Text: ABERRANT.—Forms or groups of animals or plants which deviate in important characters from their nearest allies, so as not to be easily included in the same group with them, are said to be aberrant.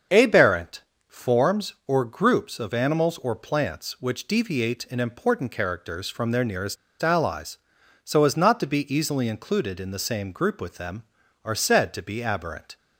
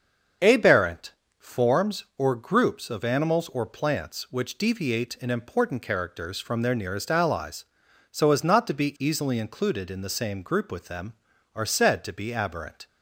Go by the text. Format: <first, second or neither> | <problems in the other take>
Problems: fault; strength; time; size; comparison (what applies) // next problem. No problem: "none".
second | starts louder than the rest; until 1.3 s; 6.5 dB; also in the second // pauses between "nearest" and "allies"; slight; at 6.7 s; 0.26 s long